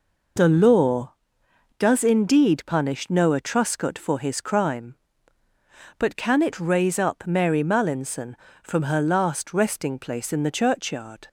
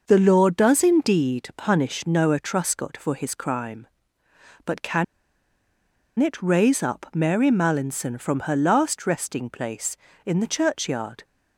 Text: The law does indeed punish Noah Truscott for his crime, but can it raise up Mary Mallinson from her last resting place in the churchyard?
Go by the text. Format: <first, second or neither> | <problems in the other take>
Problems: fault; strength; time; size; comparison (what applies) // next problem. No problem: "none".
first | pauses between "can" and "it"; at 5.0 s; 1.1 s long